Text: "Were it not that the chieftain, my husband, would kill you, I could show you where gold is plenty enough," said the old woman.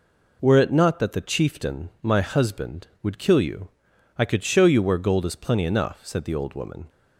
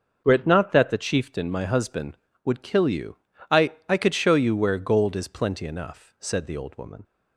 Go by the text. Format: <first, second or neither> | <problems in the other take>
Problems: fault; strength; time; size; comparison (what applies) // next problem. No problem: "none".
first | starts louder than the rest; until 1.2 s; 6.5 dB // says "I" twice; at 3.8 s